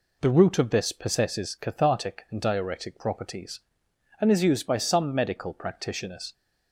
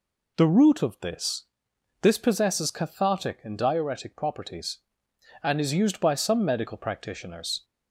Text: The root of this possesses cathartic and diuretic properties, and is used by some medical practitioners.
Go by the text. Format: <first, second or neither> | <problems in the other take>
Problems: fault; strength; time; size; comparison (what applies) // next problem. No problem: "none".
first | says "this" twice; at 2.0 s